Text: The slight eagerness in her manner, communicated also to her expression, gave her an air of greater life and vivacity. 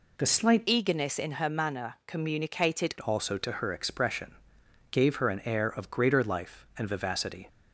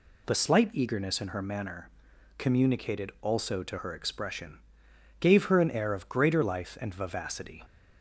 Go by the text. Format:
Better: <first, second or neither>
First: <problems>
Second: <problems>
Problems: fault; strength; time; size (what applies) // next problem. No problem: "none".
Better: second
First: changes voice from "eagerness" to "communicated"; from 0.6 to 2.9 s; 2.3 s long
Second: none